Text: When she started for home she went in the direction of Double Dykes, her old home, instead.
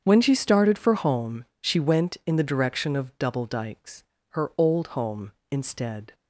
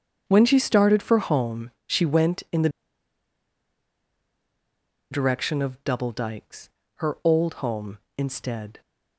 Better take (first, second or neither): first